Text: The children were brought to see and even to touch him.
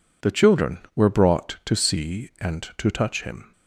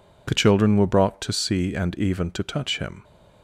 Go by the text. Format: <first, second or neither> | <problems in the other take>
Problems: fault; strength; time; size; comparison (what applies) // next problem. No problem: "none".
second | skips "even"; at 2.7 s